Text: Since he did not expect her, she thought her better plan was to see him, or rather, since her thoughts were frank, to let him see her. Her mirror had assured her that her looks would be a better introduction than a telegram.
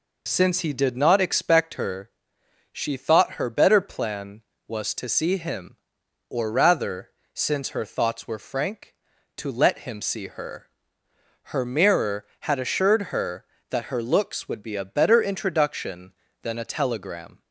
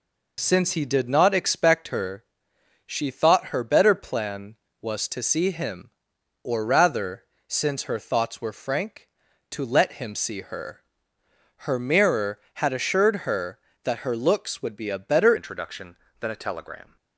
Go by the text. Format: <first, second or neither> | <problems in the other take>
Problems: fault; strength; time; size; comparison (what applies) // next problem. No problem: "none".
first | changes voice at "introduction"; from 15.3 s on; 1.6 s long